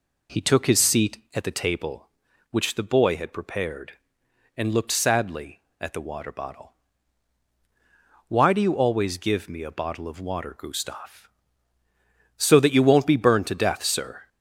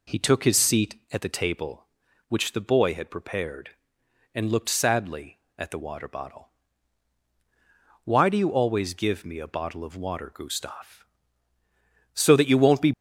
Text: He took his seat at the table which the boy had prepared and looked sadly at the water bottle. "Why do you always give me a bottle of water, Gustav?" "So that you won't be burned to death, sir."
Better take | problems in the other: first | stops before "burned to death sir"; at 12.9 s

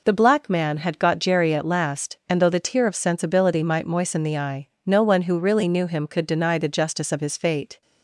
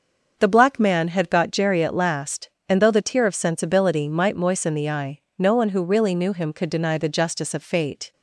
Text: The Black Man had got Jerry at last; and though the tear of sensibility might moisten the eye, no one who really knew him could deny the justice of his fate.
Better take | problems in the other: first | starts louder than the rest; noticeable; until 1.3 s; 6 dB // skips "his"; at 7.6 s

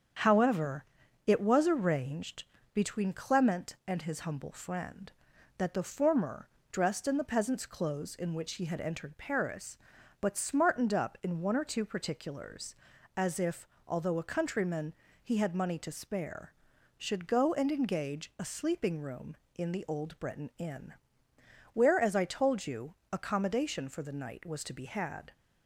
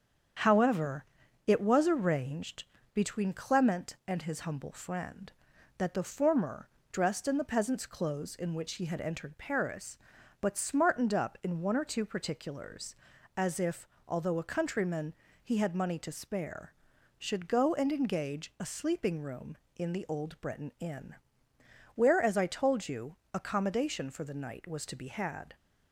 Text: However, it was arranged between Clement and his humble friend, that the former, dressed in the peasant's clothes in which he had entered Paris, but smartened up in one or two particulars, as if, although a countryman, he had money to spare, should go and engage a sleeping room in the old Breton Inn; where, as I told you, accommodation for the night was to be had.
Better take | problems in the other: neither | starts louder than the rest; strong; the same in both // pauses between "arranged" and "between"; slight; the same in both

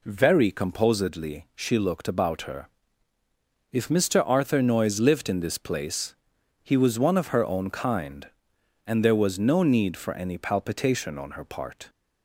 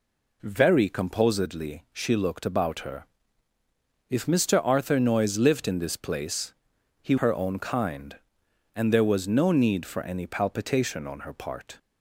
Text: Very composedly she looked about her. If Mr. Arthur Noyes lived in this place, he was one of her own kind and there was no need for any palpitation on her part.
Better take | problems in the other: first | skips "was one of"; at 7.1 s

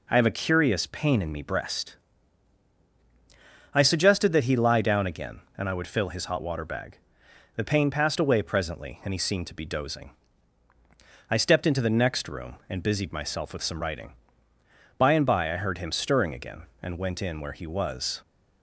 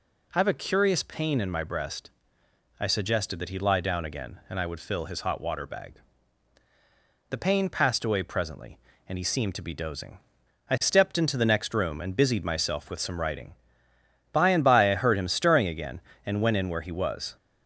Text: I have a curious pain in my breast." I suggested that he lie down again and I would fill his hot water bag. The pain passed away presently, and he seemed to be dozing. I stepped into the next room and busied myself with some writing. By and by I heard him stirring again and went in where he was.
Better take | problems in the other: second | says "me" for "my"; at 1.3 s

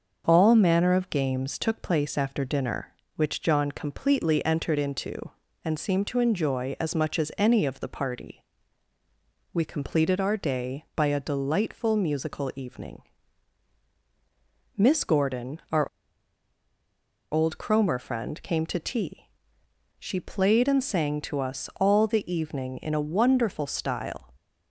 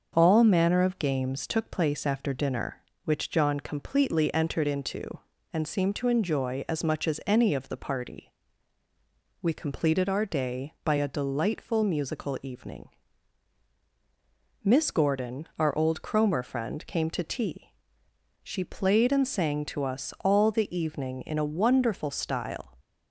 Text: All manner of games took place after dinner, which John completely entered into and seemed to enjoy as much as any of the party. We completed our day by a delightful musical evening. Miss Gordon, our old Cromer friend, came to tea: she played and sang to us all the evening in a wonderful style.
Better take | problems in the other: second | starts louder than the rest; noticeable; until 1.2 s; 6 dB; noticeable in the second // pauses between "our" and "old"; strong; at 15.8 s; 1.4 s long

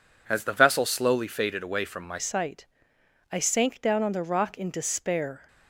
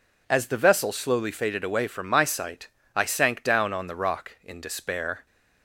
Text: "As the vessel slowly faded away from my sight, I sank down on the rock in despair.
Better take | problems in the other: second | changes voice at "sight"; from 2.1 s on; 3.3 s long

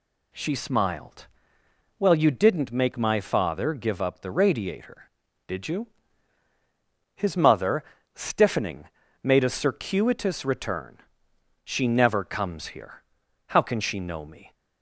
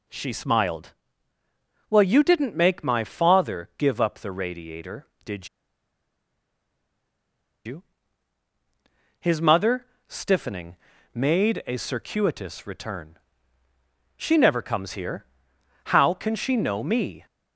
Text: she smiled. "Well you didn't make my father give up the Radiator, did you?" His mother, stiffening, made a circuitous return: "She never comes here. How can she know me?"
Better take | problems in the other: first | pauses between "did" and "you"; strong; at 5.4 s; 2.1 s long

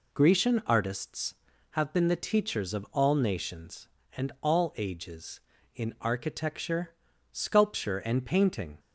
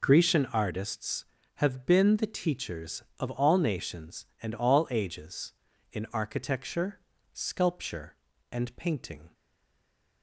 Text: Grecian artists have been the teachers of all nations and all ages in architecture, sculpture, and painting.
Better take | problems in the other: first | stays silent after the last word; slight; from 9.3 s on; 0.9 s long

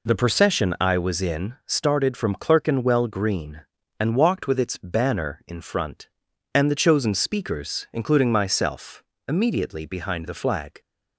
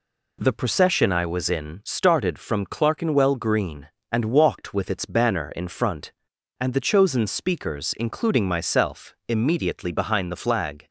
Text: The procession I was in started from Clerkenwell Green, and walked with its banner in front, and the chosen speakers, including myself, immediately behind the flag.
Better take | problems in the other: neither | none

